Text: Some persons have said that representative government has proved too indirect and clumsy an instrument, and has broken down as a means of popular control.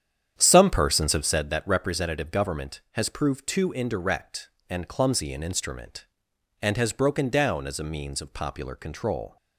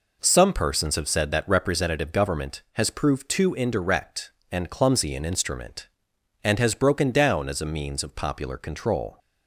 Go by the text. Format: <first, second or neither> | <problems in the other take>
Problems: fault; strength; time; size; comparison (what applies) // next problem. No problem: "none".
second | starts louder than the rest; strong; until 1.5 s; 9 dB